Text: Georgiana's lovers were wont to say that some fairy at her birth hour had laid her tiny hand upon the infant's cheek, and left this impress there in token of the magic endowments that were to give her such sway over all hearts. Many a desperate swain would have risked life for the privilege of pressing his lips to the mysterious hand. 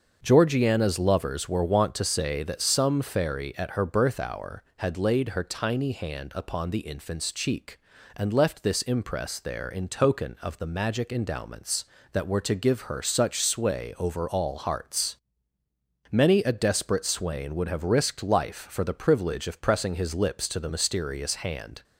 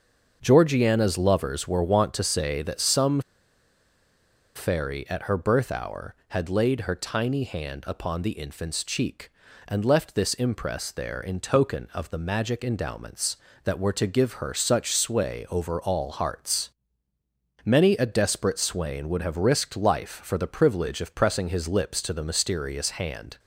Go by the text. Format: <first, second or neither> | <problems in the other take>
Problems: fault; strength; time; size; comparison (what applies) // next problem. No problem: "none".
first | starts louder than the rest; until 1.4 s; 6.5 dB; also in the first // pauses between "some" and "fairy"; strong; at 3.1 s; 1.3 s long